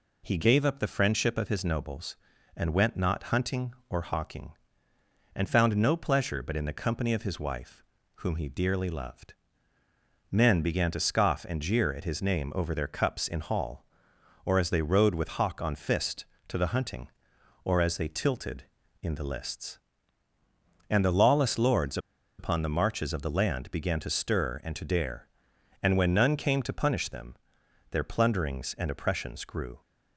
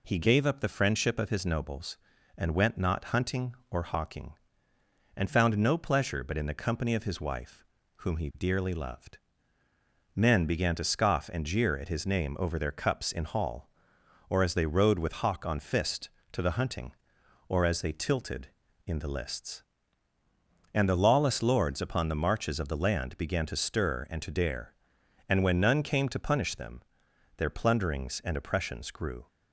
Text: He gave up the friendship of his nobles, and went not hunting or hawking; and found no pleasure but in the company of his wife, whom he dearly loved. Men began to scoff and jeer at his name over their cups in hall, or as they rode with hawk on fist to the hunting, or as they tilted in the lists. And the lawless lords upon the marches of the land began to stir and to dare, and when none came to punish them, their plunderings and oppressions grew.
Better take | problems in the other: second | pauses between "lords" and "upon"; at 21.9 s; 0.40 s long

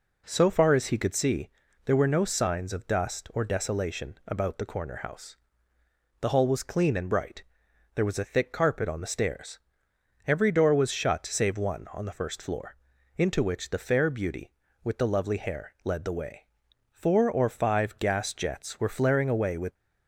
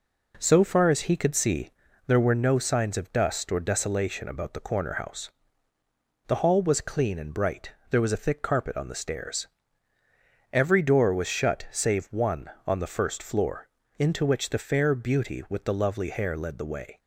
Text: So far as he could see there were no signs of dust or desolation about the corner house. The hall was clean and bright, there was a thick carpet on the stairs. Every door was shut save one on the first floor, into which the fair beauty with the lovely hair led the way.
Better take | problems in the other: second | pauses between "see" and "there"; slight; at 1.4 s; 0.36 s long; also in the second // goes on to say "Four or five gas jets were flaring away with"; strong; from 16.8 s on; 2.8 s long

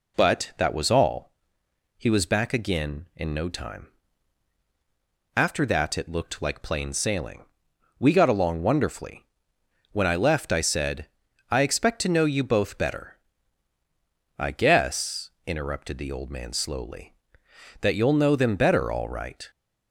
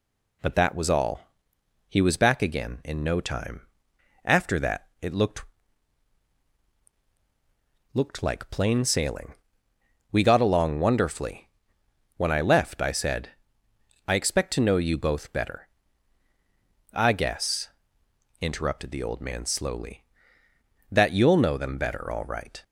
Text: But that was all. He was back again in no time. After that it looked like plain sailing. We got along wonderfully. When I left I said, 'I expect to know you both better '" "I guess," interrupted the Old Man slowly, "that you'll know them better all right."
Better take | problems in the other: first | says "looked" twice; at 7.9 s

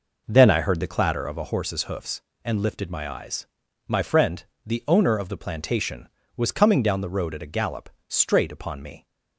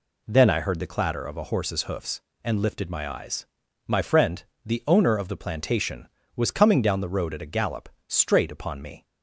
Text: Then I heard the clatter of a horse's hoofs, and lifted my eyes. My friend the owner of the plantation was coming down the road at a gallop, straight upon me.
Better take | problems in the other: second | starts louder than the rest; noticeable; until 1.6 s; 5 dB // pauses between "friend" and "the"; slight; at 4.4 s; 0.22 s long; slight in the second

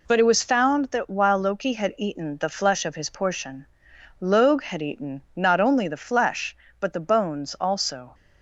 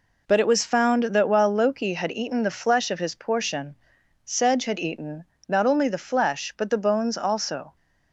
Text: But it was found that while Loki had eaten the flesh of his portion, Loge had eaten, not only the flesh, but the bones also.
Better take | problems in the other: first | says "Sedge" for "Loge"; at 4.2 s

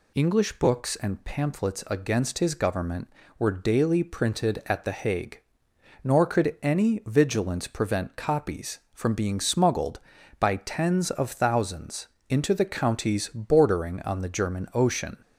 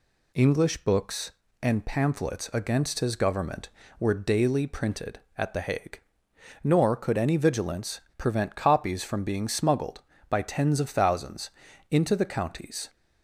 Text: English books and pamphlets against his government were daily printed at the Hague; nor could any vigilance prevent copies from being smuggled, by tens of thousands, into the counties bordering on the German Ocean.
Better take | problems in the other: first | pauses between "vigilance" and "prevent"; slight; at 8.0 s; 0.15 s long // stops before "bordering on the German Ocean"; at 12.8 s

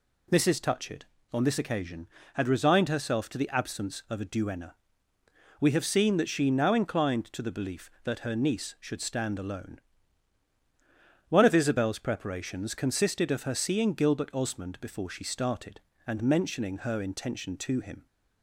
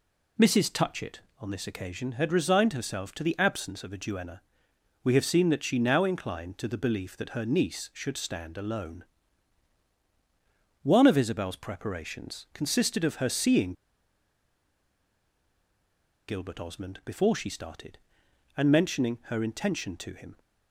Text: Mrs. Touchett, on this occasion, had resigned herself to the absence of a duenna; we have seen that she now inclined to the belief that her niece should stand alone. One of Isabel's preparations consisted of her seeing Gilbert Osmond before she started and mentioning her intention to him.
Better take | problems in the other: first | pauses between "seeing" and "Gilbert"; strong; at 13.7 s; 2.5 s long

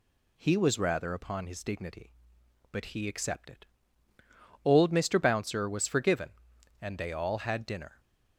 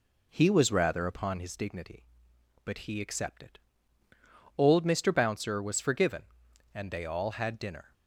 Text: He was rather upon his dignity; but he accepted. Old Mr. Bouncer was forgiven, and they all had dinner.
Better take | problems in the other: first | starts louder than the rest; slight; until 1.6 s; 3.5 dB

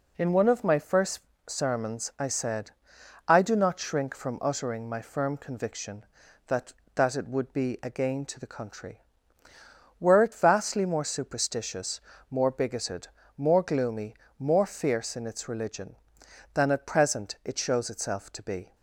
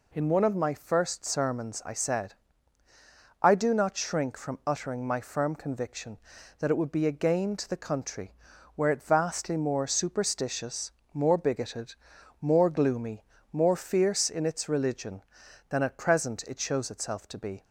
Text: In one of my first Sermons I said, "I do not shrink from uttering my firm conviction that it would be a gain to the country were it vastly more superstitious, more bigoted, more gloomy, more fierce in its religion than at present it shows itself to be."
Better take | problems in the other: second | pauses between "first" and "Sermons"; slight; at 1.1 s; 0.28 s long // says "that" twice; at 6.9 s

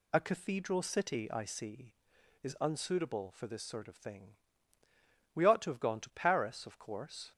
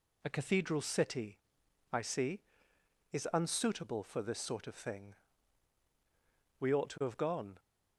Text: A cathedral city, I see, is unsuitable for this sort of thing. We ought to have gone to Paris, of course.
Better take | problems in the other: first | stops before "to Paris of course"; at 7.5 s

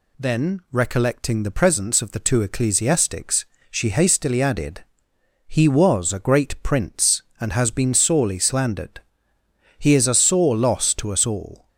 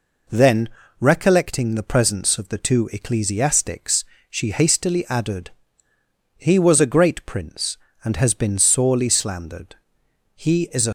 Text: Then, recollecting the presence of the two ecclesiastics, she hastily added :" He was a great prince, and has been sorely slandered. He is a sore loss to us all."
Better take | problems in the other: first | stops before "sore loss to us all"; at 10.8 s

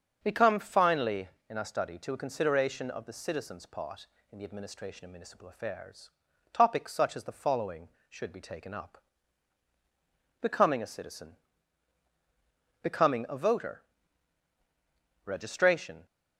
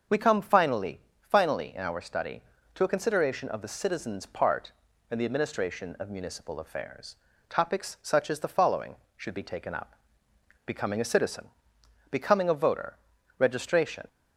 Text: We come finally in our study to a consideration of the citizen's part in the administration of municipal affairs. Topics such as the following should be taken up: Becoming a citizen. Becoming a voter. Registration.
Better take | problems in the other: first | starts louder than the rest; noticeable; until 1.3 s; 6 dB; also in the first // says "finally" twice; at 1.1 s

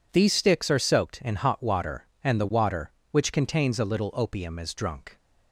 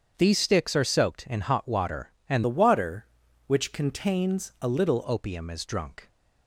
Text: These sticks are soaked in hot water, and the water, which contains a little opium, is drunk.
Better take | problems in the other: first | starts louder than the rest; strong; until 1.1 s; 7.5 dB // changes voice from "the" to "little"; from 2.4 to 5.0 s; 2.6 s long

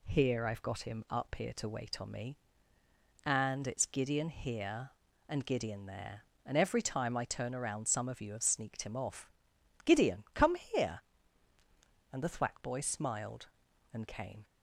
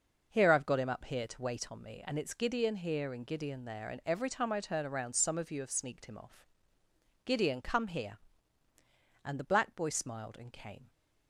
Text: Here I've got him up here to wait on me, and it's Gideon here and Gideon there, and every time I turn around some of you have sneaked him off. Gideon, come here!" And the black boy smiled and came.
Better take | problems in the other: second | says "thwack" for "black"; at 12.2 s

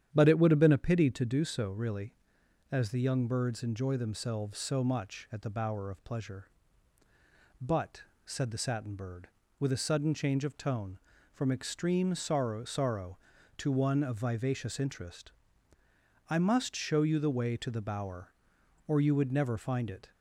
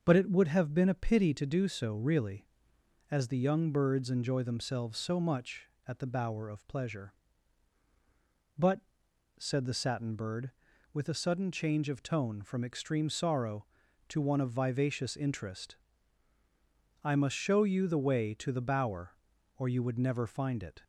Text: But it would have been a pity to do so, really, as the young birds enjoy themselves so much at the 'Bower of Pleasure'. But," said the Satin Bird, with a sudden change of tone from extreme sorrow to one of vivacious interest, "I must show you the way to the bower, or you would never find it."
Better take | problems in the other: second | starts louder than the rest; strong; until 1.1 s; 9.5 dB; also in the second // says "sorrow" twice; at 12.6 s

